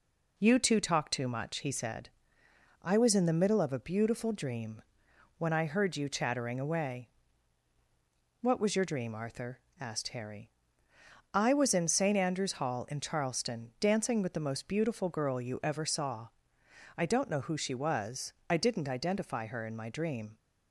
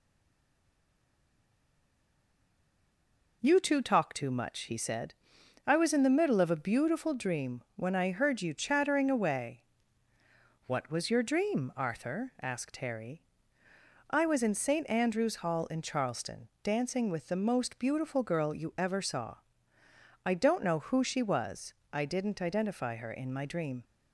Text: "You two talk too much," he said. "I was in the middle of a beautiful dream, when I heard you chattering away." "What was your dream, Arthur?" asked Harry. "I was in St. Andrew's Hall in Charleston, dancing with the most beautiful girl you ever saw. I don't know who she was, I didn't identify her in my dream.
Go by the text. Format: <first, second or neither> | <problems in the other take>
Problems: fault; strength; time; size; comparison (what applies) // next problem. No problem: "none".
first | stays silent before the first word; strong; until 3.4 s; 3.4 s long